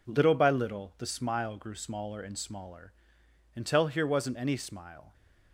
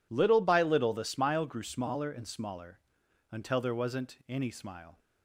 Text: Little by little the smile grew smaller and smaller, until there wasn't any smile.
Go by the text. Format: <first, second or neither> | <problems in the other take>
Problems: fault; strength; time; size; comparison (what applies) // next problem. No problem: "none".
second | says "here" for "there"; at 3.8 s